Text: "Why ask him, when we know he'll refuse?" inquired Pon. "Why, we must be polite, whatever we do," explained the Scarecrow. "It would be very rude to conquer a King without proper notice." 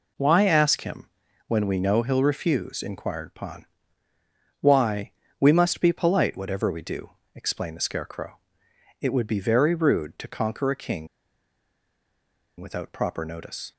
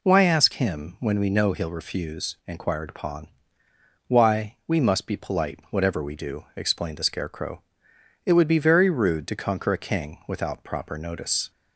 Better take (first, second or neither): second